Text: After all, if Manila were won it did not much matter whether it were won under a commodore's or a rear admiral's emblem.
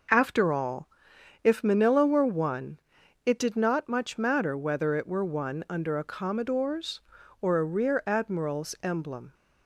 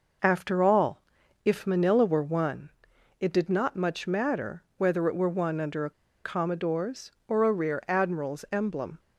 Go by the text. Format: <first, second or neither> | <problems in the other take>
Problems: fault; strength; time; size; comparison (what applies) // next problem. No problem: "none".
first | pauses between "won" and "it"; noticeable; at 2.7 s; 0.50 s long; noticeable in the first // pauses between "matter" and "whether"; slight; at 4.6 s; 0.16 s long // pauses between "a" and "commodore's"; slight; at 5.9 s; 0.33 s long